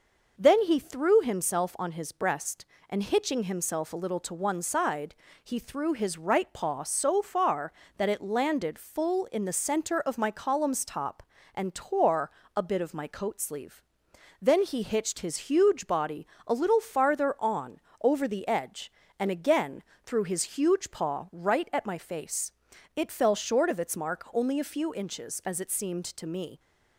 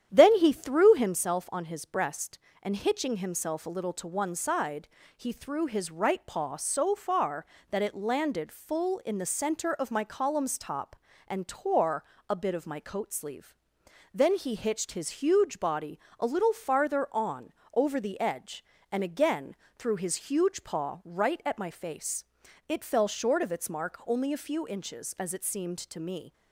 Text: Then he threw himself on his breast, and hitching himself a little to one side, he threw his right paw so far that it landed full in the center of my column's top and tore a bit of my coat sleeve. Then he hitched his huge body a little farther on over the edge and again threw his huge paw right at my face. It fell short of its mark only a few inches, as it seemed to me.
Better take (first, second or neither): first